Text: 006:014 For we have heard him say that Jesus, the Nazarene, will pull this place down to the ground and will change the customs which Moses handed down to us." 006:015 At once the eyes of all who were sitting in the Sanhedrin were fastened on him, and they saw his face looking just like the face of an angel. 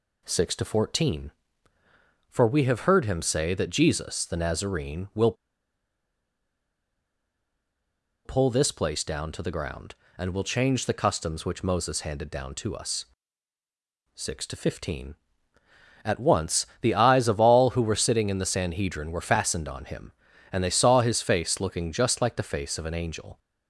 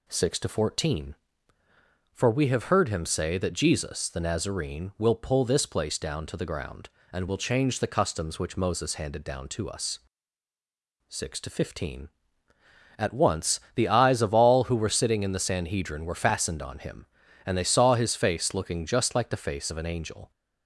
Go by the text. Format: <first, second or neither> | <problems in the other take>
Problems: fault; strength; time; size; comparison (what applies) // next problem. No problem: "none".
second | pauses between "will" and "pull"; strong; at 5.3 s; 2.9 s long // pauses between "once" and "the"; slight; at 16.6 s; 0.16 s long; slight in the second